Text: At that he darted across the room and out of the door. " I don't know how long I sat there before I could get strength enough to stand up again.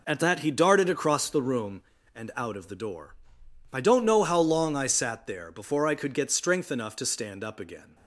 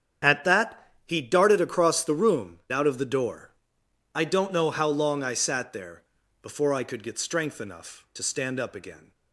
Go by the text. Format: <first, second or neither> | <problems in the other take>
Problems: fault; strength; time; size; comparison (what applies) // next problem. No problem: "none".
first | starts louder than the rest; strong; until 1.4 s; 7.5 dB // pauses between "that" and "he"; slight; at 0.8 s; 0.16 s long // skips "and"; at 2.6 s // pauses between "there" and "before"; at 6.0 s; 0.38 s long